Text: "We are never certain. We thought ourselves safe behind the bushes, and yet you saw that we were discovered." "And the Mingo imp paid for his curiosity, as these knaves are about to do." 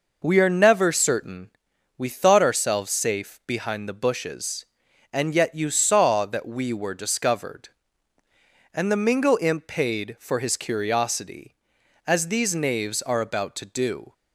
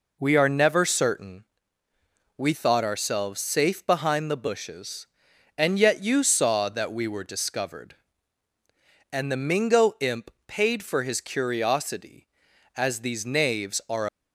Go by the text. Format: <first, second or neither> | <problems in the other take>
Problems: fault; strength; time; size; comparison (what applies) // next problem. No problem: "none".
first | pauses between "imp" and "paid"; slight; at 10.3 s; 0.18 s long // stops before "about to do"; at 14.0 s